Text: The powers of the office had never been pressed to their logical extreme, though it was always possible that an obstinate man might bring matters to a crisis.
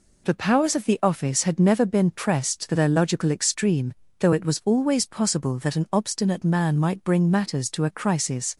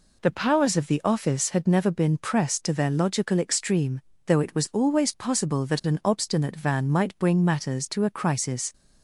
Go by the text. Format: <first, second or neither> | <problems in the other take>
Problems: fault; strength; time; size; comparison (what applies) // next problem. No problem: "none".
first | says "van" for "man"; at 6.5 s